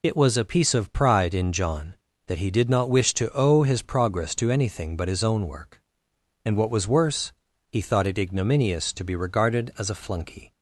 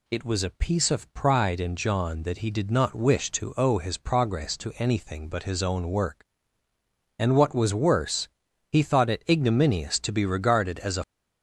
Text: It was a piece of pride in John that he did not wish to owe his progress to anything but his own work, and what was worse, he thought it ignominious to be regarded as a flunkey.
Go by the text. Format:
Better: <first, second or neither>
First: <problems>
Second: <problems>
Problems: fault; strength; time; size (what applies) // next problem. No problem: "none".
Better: first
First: none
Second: stops before "flunkey"; at 11.0 s